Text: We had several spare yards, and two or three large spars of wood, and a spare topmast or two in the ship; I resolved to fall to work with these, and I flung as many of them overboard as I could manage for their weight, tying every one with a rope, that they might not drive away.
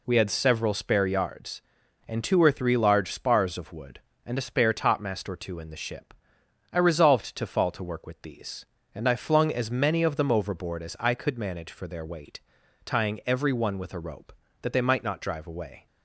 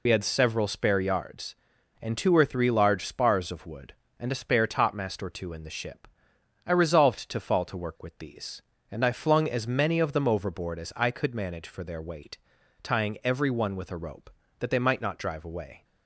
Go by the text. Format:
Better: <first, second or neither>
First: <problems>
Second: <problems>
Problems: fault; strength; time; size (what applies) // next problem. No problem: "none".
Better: first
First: none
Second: loses the start of "We"; at 0.0 s; 60 ms